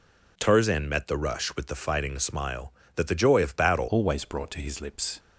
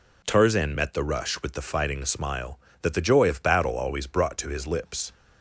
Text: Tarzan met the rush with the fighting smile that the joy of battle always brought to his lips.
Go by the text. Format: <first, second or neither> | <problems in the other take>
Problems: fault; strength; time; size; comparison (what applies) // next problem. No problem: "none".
second | changes voice at "always"; from 3.8 s on; 1.3 s long